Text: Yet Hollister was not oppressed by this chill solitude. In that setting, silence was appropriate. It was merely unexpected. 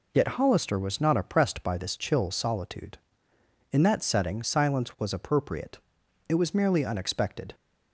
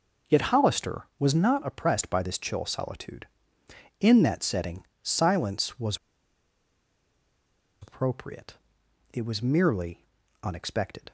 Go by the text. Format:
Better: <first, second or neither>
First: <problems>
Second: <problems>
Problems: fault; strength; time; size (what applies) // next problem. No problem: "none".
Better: first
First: none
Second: pauses between "was" and "appropriate"; strong; at 5.9 s; 1.8 s long // pauses between "merely" and "unexpected"; slight; at 10.0 s; 0.36 s long